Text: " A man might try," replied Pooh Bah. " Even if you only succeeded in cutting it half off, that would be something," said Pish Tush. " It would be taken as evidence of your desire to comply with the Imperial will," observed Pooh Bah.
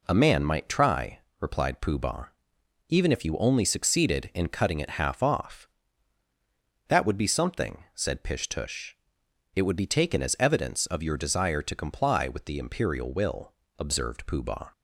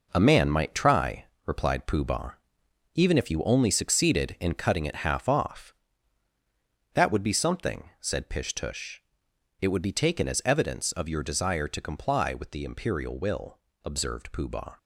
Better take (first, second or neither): first